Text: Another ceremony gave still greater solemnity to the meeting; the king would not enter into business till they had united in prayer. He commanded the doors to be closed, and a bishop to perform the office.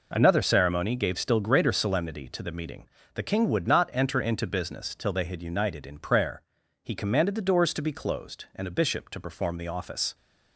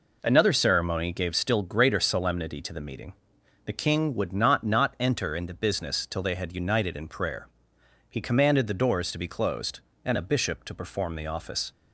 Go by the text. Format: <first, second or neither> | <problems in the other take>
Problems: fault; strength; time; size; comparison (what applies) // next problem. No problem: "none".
first | says "not" twice; at 4.6 s